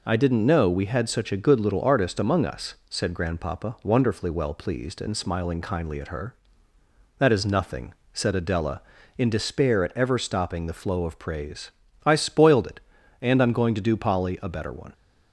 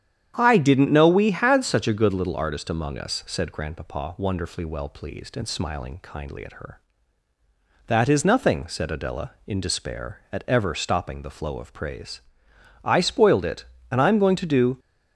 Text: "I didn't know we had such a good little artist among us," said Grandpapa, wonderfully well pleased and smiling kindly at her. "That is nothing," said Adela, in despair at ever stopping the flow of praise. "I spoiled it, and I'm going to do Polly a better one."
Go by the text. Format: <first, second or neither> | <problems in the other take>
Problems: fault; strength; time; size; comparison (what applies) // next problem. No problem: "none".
first | starts louder than the rest; strong; until 1.3 s; 9.5 dB // stops before "Polly a better one"; at 14.7 s